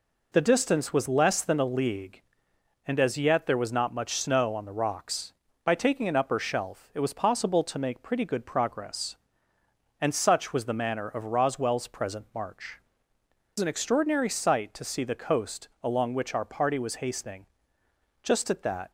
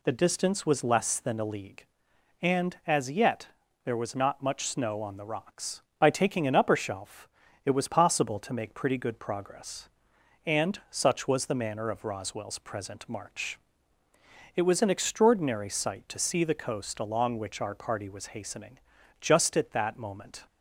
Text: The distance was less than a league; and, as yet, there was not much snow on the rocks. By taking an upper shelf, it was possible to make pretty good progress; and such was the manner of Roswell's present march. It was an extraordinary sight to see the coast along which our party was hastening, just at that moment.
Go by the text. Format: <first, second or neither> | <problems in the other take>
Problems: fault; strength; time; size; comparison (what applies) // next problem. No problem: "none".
second | stops before "moment"; at 18.8 s